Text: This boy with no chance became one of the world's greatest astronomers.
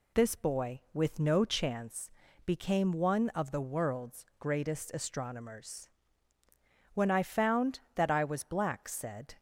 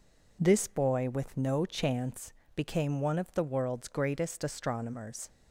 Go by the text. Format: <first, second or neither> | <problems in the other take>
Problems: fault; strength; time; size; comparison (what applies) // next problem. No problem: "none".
second | pauses between "chance" and "became"; slight; at 2.1 s; 0.34 s long; slight in the second // goes on to say "When I found that I was black said"; strong; from 6.9 s on; 2.4 s long